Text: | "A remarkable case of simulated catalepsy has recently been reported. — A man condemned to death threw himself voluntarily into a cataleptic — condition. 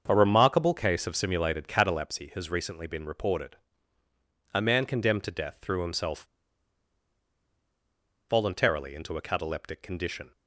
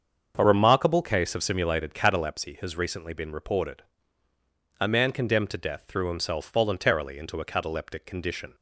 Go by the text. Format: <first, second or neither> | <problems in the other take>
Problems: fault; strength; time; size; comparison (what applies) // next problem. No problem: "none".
second | starts louder than the rest; until 1.0 s; 7 dB; also in the second // pauses between "himself" and "voluntarily"; strong; at 6.2 s; 2.0 s long